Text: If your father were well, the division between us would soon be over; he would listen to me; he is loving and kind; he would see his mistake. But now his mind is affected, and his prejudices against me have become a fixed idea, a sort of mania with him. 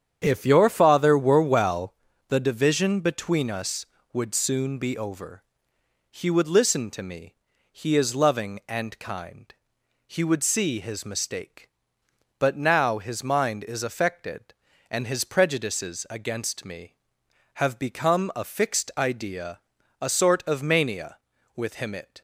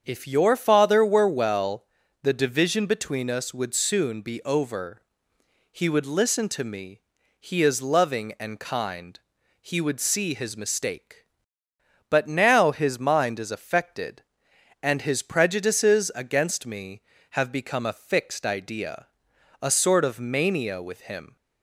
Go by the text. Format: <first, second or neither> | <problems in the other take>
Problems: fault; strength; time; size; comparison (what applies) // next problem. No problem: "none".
second | starts louder than the rest; strong; until 1.2 s; 8.5 dB; strong in the second // goes on to say "It"; slight; from 21.9 s on; 0.28 s long